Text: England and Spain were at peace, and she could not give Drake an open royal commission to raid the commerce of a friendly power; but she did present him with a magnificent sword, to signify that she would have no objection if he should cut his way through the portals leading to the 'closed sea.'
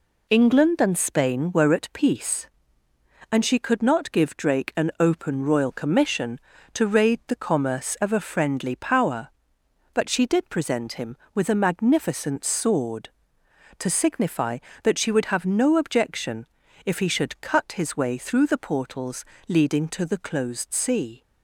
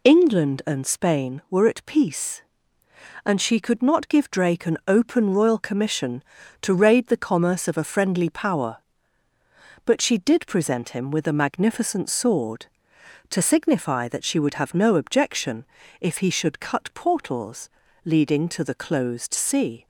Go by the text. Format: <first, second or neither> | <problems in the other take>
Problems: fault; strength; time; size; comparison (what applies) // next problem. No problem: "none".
first | pauses between "objection" and "if"; slight; at 15.6 s; 0.34 s long; also in the first // skips "his way through the"; at 16.9 s // pauses between "portals" and "leading"; slight; at 17.7 s; 0.34 s long; slight in the first